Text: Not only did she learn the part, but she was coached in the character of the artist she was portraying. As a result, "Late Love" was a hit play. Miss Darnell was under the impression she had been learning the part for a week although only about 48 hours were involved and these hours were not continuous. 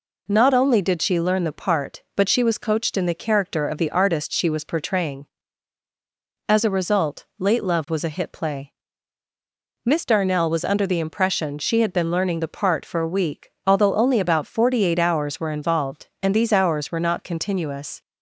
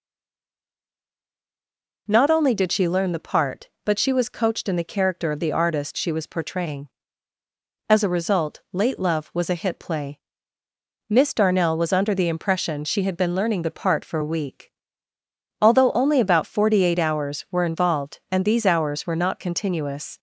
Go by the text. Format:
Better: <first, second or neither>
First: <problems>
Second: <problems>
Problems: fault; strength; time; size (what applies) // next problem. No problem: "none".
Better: first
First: pauses between "week" and "although"; slight; at 13.5 s; 0.16 s long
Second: stays silent before the first word; noticeable; until 2.0 s; 2.0 s long // pauses between "week" and "although"; noticeable; at 14.7 s; 0.90 s long